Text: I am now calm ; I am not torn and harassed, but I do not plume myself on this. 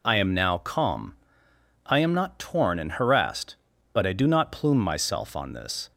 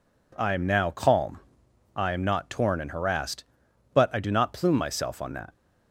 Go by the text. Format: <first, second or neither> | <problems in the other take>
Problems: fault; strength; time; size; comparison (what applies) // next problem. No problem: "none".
first | says "that" for "this"; at 5.3 s